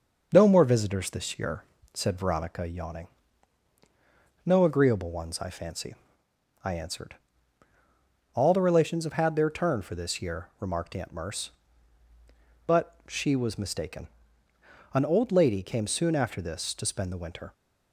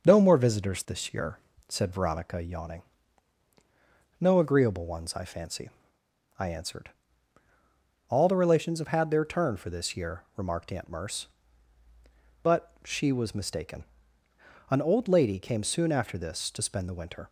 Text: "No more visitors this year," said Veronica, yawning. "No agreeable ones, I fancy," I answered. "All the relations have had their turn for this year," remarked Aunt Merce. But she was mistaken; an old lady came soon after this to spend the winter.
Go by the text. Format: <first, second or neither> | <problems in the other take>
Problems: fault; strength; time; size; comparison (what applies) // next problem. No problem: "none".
neither | starts louder than the rest; noticeable; the same in both